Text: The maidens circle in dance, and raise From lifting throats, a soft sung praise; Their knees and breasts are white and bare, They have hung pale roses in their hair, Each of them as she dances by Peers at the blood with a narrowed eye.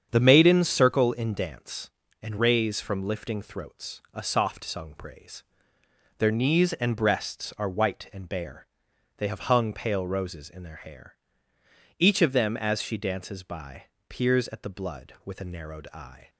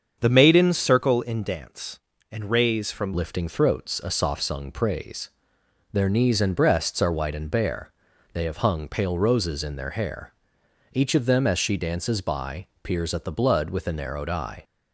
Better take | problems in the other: first | starts louder than the rest; until 1.2 s; 7 dB; strong in the first // changes voice at "lifting"; from 3.1 s on; 11.5 s long // pauses between "by" and "Peers"; slight; at 12.6 s; 0.16 s long; slight in the first

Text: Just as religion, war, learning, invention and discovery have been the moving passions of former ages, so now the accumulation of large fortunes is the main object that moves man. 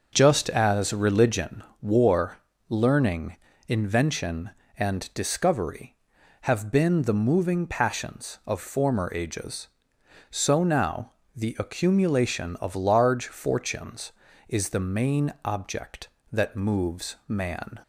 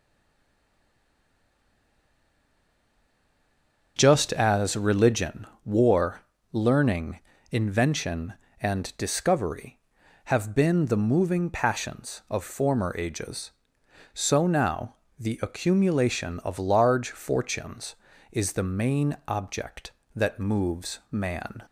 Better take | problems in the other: first | stays silent before the first word; strong; until 3.9 s; 3.9 s long // starts louder than the rest; noticeable; until 5.0 s; 6 dB; noticeable in the first // pauses between "now" and "the"; slight; at 14.9 s; 0.24 s long; slight in the first

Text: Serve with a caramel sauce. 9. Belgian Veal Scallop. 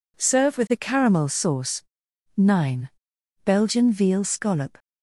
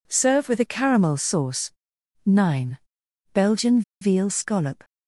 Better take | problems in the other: first | pauses between "Belgian" and "Veal"; slight; at 3.8 s; 0.20 s long

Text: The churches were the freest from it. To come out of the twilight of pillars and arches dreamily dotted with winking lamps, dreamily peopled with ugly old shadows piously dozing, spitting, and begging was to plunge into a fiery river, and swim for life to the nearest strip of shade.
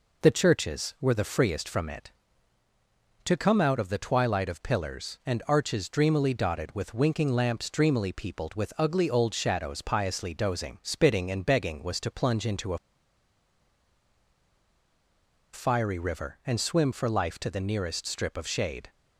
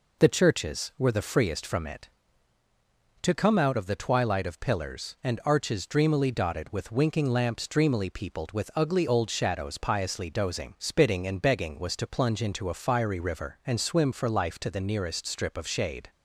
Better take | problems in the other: second | pauses between "a" and "fiery"; strong; at 12.7 s; 2.7 s long

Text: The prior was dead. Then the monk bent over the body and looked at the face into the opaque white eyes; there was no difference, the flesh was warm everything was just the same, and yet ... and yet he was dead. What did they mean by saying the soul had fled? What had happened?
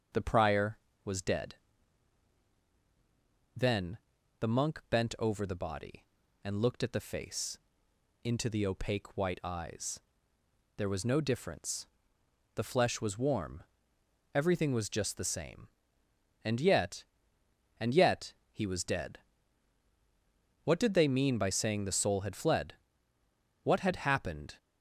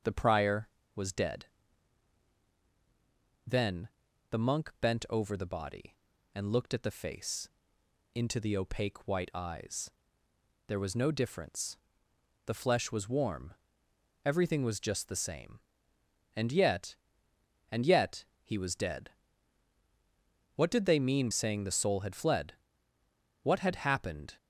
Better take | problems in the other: first | starts louder than the rest; until 1.3 s; 6.5 dB; also in the first // pauses between "Then" and "the"; at 3.8 s; 0.44 s long; also in the first // pauses between "face" and "into"; noticeable; at 7.4 s; 0.64 s long; noticeable in the first // pauses between "warm" and "everything"; noticeable; at 13.5 s; 0.72 s long; noticeable in the first // pauses between "yet" and "he"; slight; at 18.2 s; 0.22 s long; slight in the first // skips "by"; at 21.2 s

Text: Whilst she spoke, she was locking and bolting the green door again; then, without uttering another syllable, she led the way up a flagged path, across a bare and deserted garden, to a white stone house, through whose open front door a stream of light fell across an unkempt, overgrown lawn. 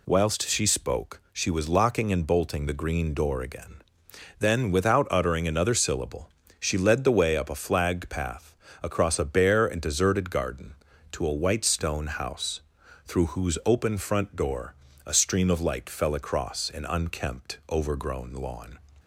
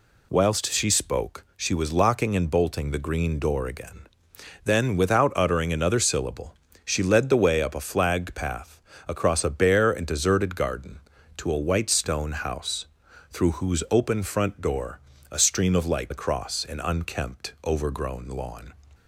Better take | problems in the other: first | pauses between "door" and "a"; slight; at 14.9 s; 0.32 s long; slight in the first // skips "fell"; at 16.1 s

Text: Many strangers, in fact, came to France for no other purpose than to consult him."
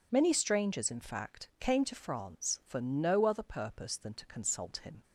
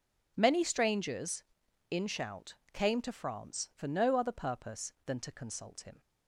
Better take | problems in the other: first | says "shout" for "fact"; at 2.0 s

